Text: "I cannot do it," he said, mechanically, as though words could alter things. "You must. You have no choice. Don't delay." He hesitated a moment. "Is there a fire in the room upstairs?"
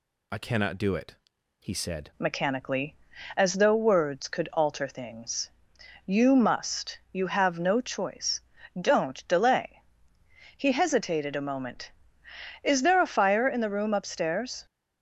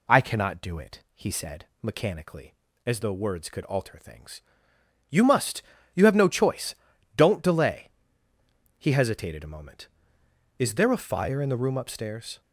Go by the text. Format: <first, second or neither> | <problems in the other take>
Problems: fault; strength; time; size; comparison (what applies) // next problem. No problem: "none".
second | changes voice at "mechanically"; from 2.1 s on; 12.5 s long